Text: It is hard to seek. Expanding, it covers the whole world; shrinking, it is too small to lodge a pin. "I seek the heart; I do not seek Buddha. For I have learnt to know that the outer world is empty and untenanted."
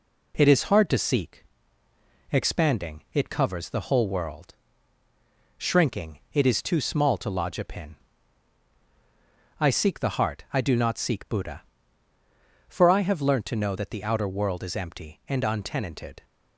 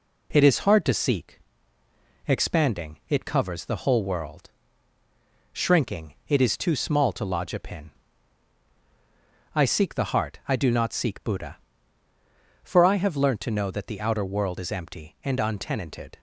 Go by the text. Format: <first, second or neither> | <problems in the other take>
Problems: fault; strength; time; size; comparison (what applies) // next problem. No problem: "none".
neither | none